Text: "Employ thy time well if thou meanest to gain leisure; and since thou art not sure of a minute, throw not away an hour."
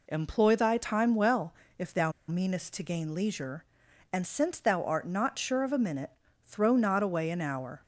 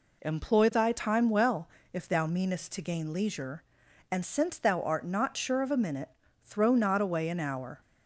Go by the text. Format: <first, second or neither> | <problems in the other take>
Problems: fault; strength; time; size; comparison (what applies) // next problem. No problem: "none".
second | pauses between "well" and "if"; slight; at 1.5 s; 0.28 s long; slight in the second // pauses between "thou" and "meanest"; slight; at 2.1 s; 0.16 s long